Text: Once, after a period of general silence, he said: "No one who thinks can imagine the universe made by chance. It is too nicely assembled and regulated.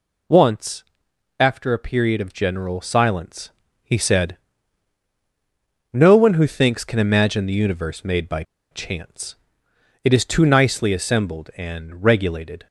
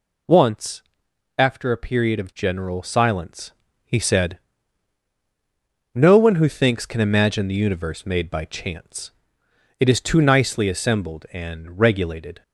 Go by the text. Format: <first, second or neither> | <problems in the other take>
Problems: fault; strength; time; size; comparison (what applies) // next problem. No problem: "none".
second | pauses between "by" and "chance"; slight; at 8.4 s; 0.28 s long